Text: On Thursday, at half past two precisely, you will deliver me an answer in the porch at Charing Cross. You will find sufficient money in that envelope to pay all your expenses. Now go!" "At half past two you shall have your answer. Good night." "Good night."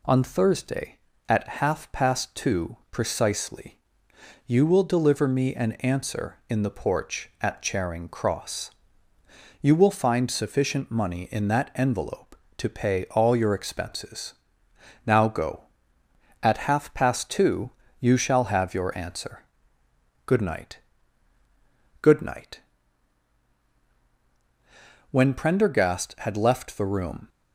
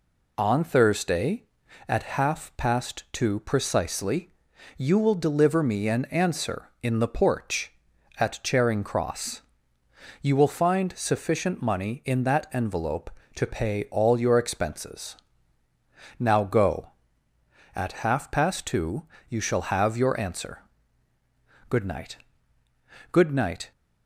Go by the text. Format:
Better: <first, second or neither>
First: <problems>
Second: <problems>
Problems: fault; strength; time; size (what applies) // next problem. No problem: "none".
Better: second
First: pauses between "two" and "you"; slight; at 17.7 s; 0.30 s long // goes on to say "When Prendergast had left the room"; strong; from 25.1 s on; 2.1 s long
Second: pauses between "two" and "you"; slight; at 19.0 s; 0.24 s long